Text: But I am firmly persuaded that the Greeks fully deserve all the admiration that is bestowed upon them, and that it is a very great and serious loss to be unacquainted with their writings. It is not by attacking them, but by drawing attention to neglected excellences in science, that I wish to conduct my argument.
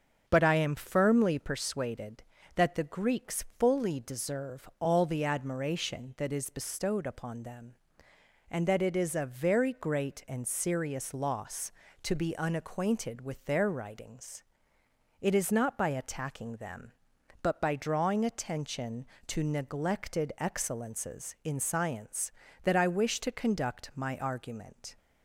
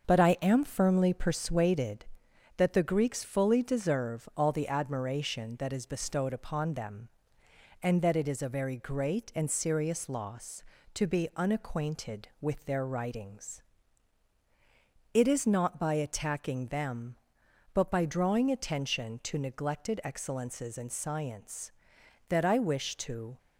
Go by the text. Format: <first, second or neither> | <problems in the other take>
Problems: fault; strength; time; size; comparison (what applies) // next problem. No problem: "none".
first | starts louder than the rest; until 1.1 s; 6.5 dB; also in the first // stops before "conduct my argument"; at 23.3 s